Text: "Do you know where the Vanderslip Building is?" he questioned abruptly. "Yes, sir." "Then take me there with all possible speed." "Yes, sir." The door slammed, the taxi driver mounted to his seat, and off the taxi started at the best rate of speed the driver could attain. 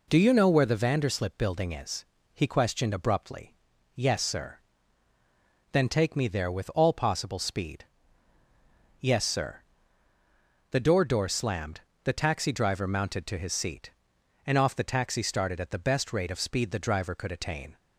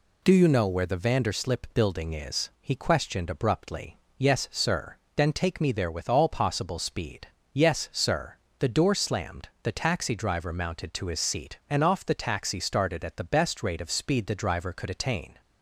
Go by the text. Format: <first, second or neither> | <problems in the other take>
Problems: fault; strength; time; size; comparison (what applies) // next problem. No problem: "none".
second | says "door" twice; at 11.0 s